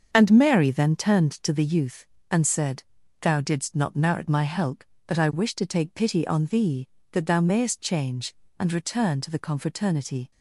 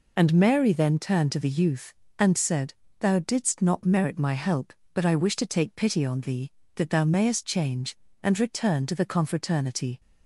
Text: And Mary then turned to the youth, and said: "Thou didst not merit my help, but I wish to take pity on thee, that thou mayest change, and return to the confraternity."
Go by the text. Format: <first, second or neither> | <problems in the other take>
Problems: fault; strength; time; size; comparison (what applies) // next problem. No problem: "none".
second | starts louder than the rest; until 1.6 s; 7 dB